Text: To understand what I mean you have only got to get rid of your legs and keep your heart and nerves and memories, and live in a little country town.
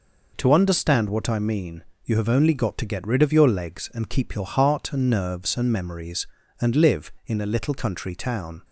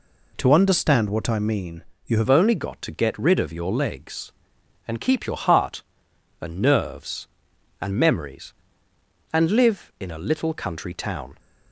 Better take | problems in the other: first | pauses between "mean" and "you"; slight; at 1.8 s; 0.24 s long; slight in the first // changes voice at "only"; from 2.2 s on; 9.1 s long

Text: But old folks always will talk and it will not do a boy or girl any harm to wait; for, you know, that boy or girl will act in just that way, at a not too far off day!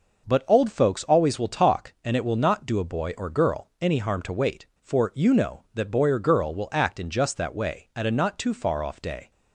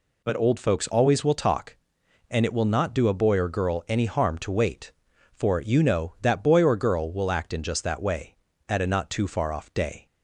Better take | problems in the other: neither | none

